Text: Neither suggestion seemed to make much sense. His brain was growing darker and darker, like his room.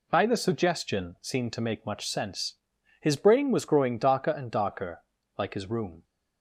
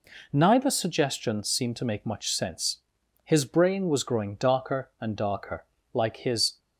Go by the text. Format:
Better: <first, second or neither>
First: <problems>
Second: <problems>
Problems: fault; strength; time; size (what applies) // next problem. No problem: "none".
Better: first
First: none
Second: stops before "room"; at 6.5 s